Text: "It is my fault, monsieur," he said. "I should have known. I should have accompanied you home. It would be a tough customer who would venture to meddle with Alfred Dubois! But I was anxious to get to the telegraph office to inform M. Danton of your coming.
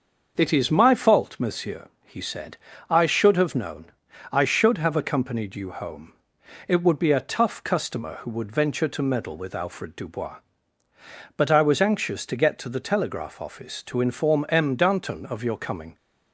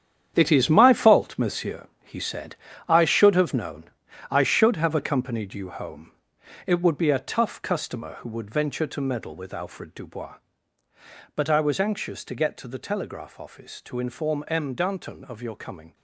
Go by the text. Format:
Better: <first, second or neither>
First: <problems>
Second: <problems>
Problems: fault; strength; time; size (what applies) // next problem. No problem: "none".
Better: first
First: starts louder than the rest; until 1.3 s; 6.5 dB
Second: gets quieter; strong; throughout; 11 dB // starts louder than the rest; strong; until 1.3 s; 9 dB